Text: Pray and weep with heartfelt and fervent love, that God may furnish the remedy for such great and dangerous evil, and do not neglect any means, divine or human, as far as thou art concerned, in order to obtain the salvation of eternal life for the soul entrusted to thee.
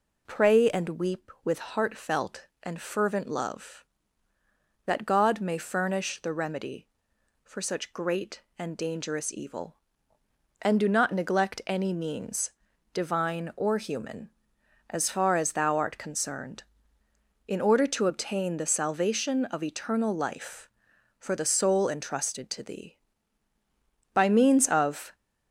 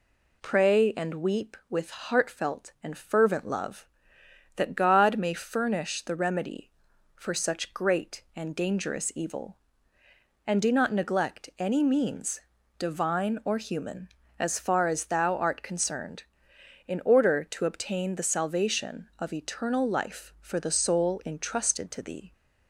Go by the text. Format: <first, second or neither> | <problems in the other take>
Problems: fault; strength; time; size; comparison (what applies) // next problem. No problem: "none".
second | goes on to say "By means of"; noticeable; from 24.1 s on; 1.0 s long